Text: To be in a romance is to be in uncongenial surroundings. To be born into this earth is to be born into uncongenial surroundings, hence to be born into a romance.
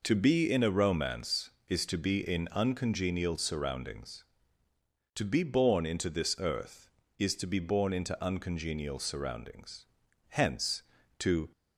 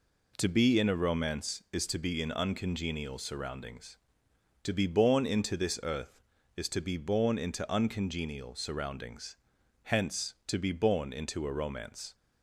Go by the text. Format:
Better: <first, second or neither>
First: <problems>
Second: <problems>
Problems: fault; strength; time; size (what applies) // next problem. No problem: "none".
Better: second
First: stops before "be born into a romance"; at 11.5 s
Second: none